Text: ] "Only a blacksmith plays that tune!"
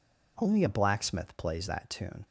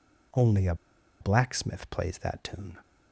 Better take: first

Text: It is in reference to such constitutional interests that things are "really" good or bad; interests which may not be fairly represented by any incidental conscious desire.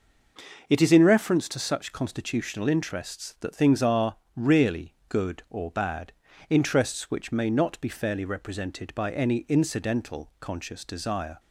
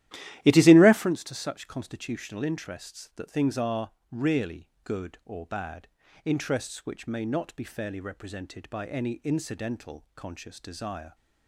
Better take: first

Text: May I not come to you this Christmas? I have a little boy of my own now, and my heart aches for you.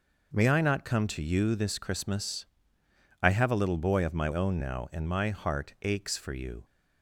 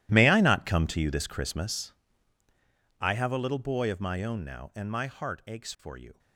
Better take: first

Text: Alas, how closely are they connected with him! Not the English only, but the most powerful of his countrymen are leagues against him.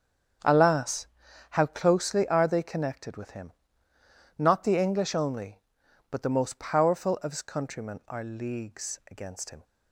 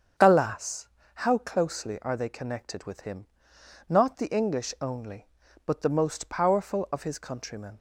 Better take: first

